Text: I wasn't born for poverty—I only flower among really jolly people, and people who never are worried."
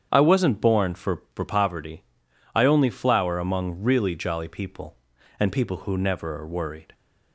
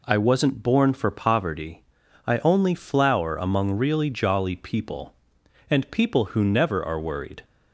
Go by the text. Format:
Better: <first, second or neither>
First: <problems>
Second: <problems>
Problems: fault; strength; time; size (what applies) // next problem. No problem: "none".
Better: second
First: starts louder than the rest; strong; until 1.1 s; 8 dB // says "for" twice; at 1.3 s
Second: none